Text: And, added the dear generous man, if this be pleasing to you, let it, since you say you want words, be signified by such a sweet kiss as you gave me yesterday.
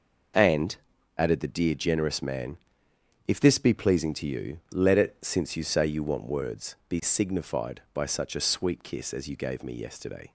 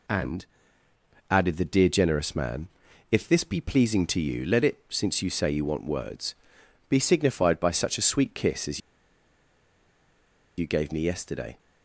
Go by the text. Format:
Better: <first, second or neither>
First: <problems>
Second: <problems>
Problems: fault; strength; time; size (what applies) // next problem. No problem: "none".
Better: first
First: none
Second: pauses between "as" and "you"; strong; at 8.8 s; 1.7 s long